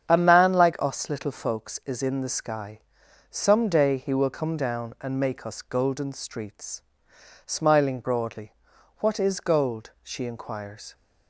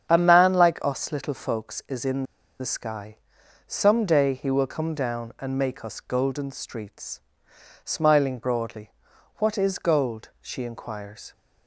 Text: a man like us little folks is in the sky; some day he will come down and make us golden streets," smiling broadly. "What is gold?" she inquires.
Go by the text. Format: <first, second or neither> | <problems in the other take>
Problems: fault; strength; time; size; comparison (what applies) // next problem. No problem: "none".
first | starts louder than the rest; strong; until 1.1 s; 8 dB; strong in the first // pauses between "in" and "the"; slight; at 2.2 s; 0.35 s long